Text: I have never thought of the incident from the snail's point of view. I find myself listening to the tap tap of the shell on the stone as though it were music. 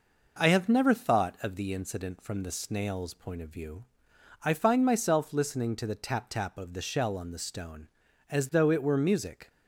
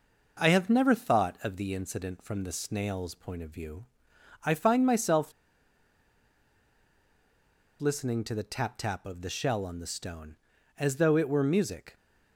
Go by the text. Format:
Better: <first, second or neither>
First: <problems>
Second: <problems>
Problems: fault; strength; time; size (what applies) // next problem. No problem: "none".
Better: first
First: none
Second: pauses between "myself" and "listening"; strong; at 5.3 s; 2.4 s long